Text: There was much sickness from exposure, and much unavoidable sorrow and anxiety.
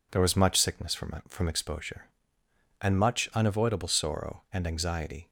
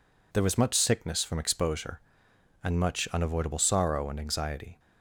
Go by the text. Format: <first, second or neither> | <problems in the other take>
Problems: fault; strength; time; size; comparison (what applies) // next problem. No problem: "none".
second | says "from" twice; at 1.2 s